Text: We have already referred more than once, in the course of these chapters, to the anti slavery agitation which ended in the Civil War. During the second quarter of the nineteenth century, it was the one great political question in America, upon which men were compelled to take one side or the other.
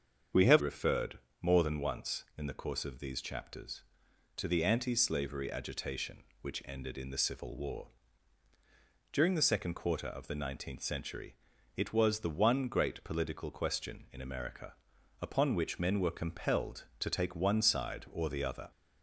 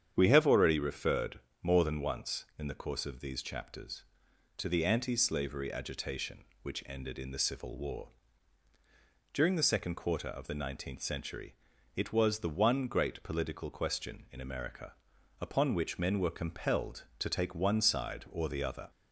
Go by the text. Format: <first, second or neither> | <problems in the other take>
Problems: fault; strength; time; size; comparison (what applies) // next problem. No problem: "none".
second | starts louder than the rest; strong; until 1.5 s; 7 dB; strong in the second // skips "already"; at 0.6 s // pauses between "referred" and "more"; slight; at 1.1 s; 0.22 s long; slight in the second